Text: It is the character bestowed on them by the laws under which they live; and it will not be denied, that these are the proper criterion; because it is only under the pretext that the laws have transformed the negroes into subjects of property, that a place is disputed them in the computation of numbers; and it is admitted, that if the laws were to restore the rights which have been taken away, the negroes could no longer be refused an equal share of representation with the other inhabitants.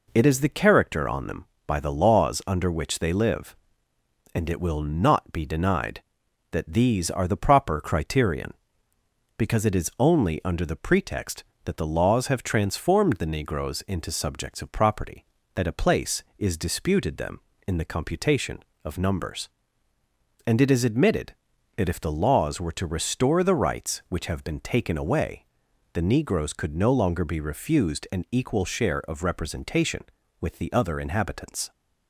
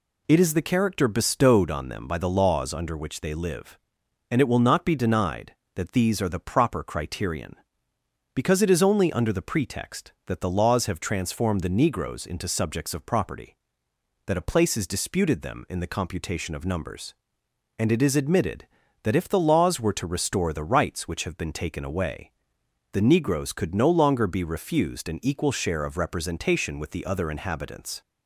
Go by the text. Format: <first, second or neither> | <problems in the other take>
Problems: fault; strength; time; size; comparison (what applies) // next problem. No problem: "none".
second | skips "bestowed"; at 1.0 s